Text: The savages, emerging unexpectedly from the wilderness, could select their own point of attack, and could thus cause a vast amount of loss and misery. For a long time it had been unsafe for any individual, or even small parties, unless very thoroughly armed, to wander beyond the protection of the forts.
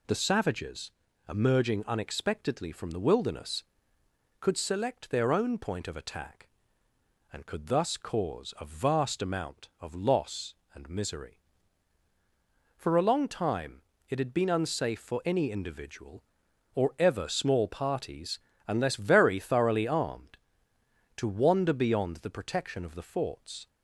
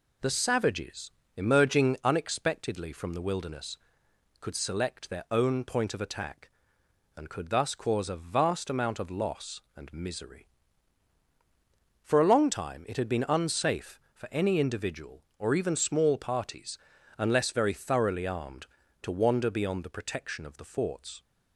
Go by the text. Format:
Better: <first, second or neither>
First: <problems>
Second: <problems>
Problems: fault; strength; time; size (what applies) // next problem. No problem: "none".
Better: second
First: pauses between "time" and "it"; slight; at 13.8 s; 0.28 s long // says "ever" for "even"; at 16.9 s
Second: none